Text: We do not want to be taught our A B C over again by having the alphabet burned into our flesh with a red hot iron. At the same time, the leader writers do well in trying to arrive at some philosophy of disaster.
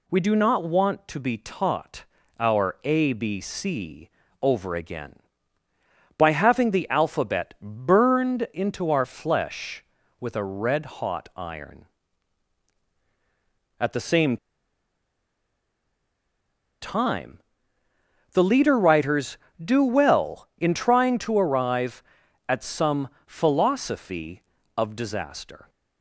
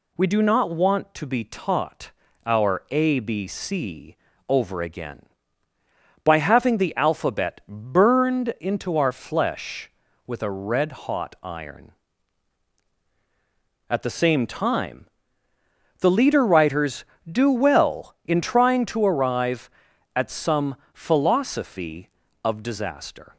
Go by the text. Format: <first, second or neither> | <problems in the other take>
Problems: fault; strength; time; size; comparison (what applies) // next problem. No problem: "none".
second | pauses between "taught" and "our"; slight; at 2.0 s; 0.34 s long; slight in the second // pauses between "C" and "over"; slight; at 4.0 s; 0.34 s long; slight in the second // pauses between "same" and "time"; strong; at 14.3 s; 2.4 s long // pauses between "some" and "philosophy"; slight; at 23.0 s; 0.18 s long; slight in the second